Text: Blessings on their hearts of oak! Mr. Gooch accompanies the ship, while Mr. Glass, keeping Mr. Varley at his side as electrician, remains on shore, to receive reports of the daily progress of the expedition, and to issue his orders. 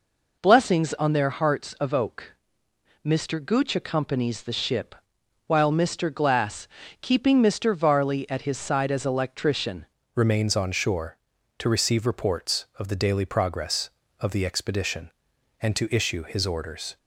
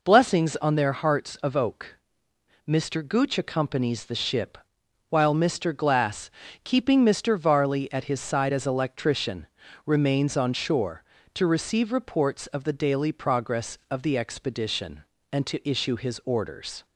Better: second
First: changes voice at "remains"; from 10.1 s on; 6.8 s long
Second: none

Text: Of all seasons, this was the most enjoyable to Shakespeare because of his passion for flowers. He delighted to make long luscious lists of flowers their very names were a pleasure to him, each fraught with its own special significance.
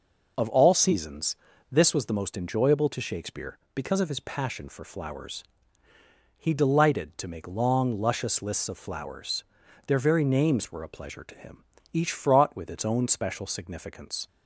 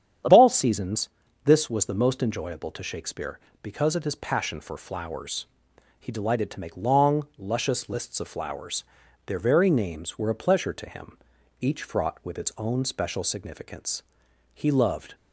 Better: first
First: pauses between "flowers" and "their"; at 9.4 s; 0.44 s long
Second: starts louder than the rest; strong; until 1.6 s; 8.5 dB // pauses between "flowers" and "their"; at 8.8 s; 0.42 s long // goes on to say "He loved"; noticeable; from 14.5 s on; 0.62 s long

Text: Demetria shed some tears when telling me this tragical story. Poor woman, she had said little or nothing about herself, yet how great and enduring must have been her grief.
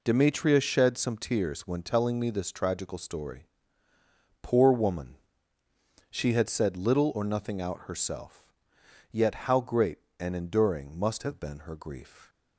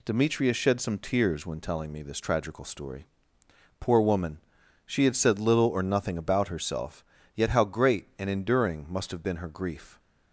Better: second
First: says "out" for "about"; at 7.6 s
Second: none

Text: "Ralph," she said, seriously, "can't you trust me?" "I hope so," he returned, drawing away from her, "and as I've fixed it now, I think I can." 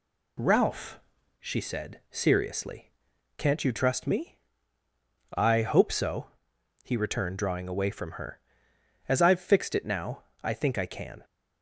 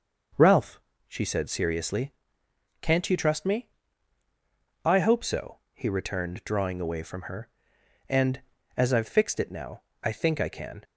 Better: second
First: skips "and"; at 8.7 s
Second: none

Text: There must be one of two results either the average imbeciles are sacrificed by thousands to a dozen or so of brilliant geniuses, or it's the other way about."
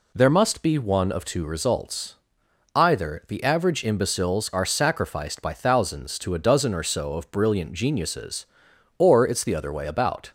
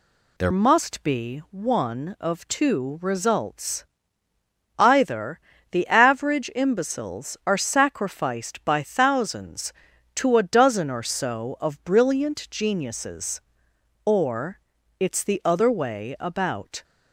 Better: first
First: pauses between "results" and "either"; noticeable; at 2.1 s; 0.60 s long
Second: changes voice at "must"; from 0.5 s on; 16.3 s long // pauses between "results" and "either"; noticeable; at 3.8 s; 0.92 s long // pauses between "either" and "the"; slight; at 5.3 s; 0.32 s long // pauses between "or" and "it's"; at 14.5 s; 0.40 s long

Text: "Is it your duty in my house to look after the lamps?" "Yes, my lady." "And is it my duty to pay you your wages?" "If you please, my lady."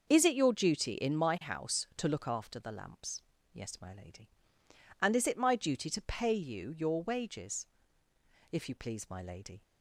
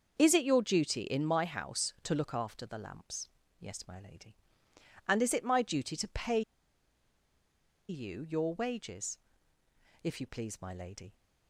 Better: first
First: starts louder than the rest; until 1.1 s; 6 dB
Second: starts louder than the rest; until 1.1 s; 6 dB // pauses between "pay" and "you"; strong; at 6.4 s; 1.4 s long

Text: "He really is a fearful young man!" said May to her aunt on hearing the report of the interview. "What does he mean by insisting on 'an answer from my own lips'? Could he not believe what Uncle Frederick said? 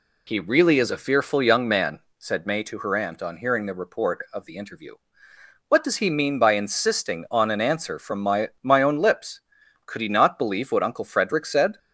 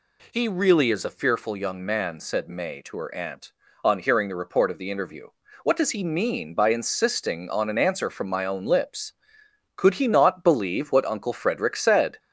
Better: second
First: says "my" twice; at 8.6 s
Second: none

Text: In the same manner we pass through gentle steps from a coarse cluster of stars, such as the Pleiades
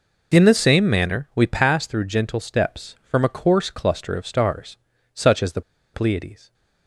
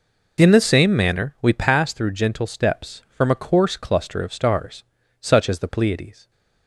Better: second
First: pauses between "the" and "Pleiades"; slight; at 5.6 s; 0.33 s long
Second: none

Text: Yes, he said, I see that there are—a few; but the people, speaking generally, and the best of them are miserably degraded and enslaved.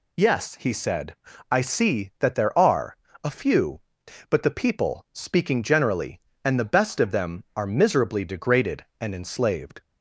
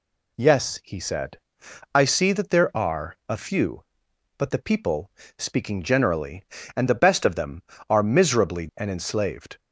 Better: first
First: none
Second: skips "degraded"; at 8.7 s

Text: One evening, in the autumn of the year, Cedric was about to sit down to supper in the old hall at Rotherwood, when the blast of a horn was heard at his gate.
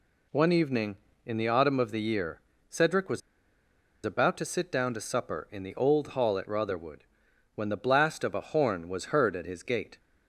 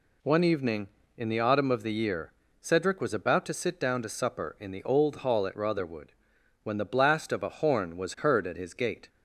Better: second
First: pauses between "was" and "about"; noticeable; at 3.2 s; 0.85 s long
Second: none

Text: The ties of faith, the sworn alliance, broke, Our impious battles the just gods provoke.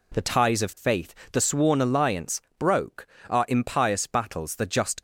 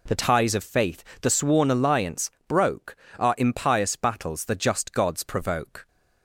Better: second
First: stops before "gods provoke"; at 4.9 s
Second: none

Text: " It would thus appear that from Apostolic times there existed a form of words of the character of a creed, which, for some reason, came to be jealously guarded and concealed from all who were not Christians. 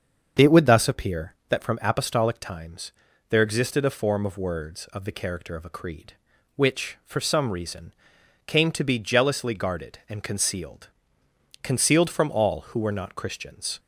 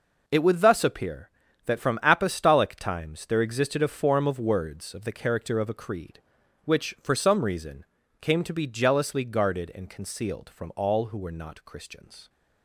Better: second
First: starts louder than the rest; until 1.5 s; 7 dB // pauses between "times" and "there"; at 2.9 s; 0.38 s long // says "concealed" twice; at 11.6 s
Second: none

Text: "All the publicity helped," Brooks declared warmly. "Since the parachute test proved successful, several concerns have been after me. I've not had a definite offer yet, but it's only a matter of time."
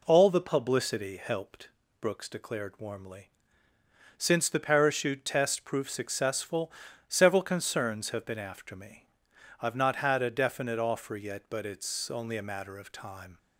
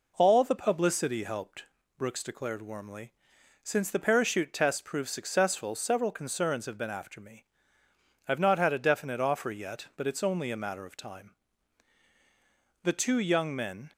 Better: first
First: none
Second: goes on to say "The two young men"; noticeable; from 12.8 s on; 1.0 s long

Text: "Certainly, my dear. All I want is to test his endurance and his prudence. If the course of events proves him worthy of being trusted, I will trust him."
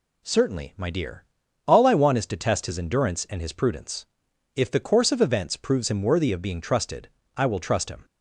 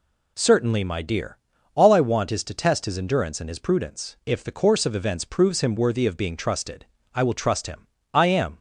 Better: first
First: none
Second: goes on to say "I am"; slight; from 8.1 s on; 0.44 s long

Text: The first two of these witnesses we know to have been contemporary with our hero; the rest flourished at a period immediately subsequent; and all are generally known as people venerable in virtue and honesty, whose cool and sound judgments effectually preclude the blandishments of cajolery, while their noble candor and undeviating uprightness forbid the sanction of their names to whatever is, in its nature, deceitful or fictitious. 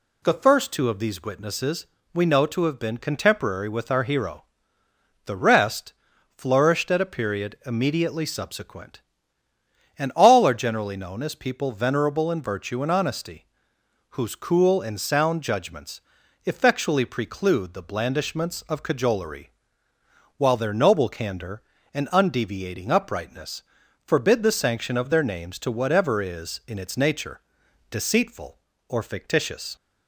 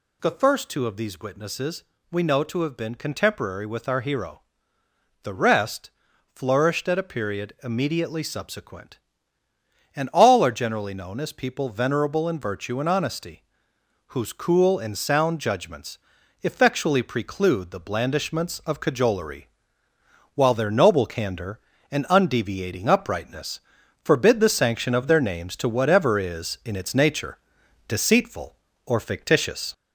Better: first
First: pauses between "witnesses" and "we"; slight; at 1.8 s; 0.28 s long // pauses between "rest" and "flourished"; noticeable; at 5.9 s; 0.46 s long // pauses between "judgments" and "effectually"; noticeable; at 15.9 s; 0.46 s long // pauses between "uprightness" and "forbid"; at 23.6 s; 0.44 s long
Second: gets louder; slight; throughout; 3.5 dB // pauses between "witnesses" and "we"; slight; at 1.8 s; 0.28 s long // pauses between "rest" and "flourished"; noticeable; at 5.8 s; 0.46 s long // pauses between "judgments" and "effectually"; noticeable; at 15.9 s; 0.46 s long // pauses between "uprightness" and "forbid"; at 23.5 s; 0.44 s long

